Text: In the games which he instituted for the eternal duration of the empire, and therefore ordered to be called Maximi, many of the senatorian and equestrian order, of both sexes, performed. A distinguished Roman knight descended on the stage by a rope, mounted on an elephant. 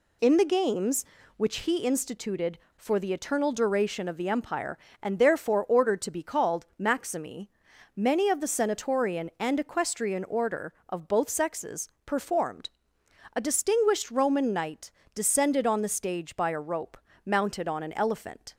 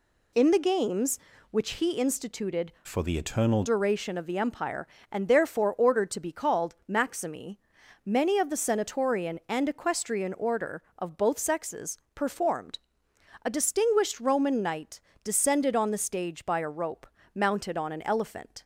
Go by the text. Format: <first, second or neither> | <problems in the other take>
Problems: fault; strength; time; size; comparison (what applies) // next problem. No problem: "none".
first | changes voice from "for" to "eternal"; from 2.8 to 3.6 s; 0.8 s long // pauses between "called" and "Maximi"; slight; at 6.7 s; 0.16 s long; slight in the first // pauses between "knight" and "descended"; slight; at 14.9 s; 0.24 s long; slight in the first